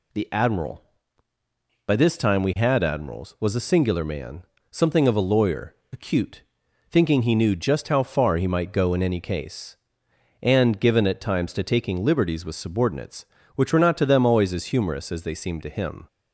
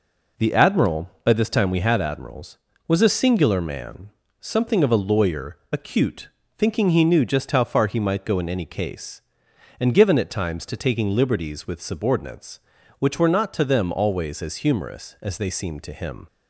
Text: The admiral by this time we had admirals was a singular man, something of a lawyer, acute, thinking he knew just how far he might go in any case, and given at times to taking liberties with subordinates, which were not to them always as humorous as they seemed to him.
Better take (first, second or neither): neither